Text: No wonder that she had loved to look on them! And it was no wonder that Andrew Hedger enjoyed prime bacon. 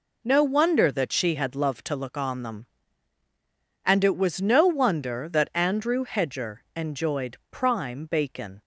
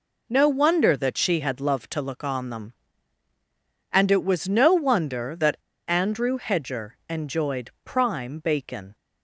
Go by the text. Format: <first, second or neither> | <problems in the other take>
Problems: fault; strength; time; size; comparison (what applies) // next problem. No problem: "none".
first | pauses between "that" and "Andrew"; slight; at 5.5 s; 0.30 s long